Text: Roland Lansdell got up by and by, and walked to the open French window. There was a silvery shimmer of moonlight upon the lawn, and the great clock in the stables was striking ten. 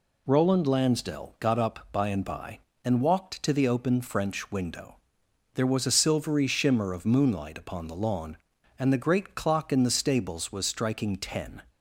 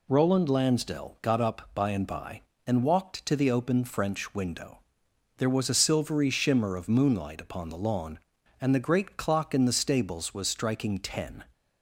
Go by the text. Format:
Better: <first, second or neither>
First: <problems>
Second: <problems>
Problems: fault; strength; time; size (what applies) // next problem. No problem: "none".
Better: neither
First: none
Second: none